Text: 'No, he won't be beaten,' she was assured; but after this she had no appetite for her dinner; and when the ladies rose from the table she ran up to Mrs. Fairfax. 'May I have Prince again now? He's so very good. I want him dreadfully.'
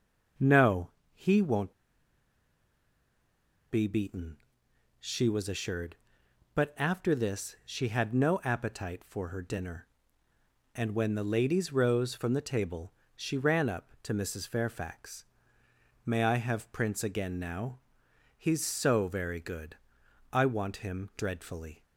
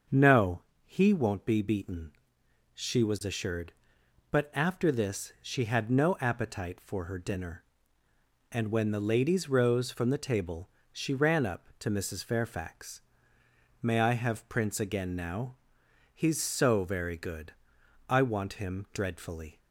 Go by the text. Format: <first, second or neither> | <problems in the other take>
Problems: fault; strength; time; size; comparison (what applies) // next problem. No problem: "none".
second | starts louder than the rest; until 1.6 s; 6.5 dB; also in the second // pauses between "won't" and "be"; strong; at 1.7 s; 1.9 s long // pauses between "table" and "she"; slight; at 12.9 s; 0.24 s long; slight in the second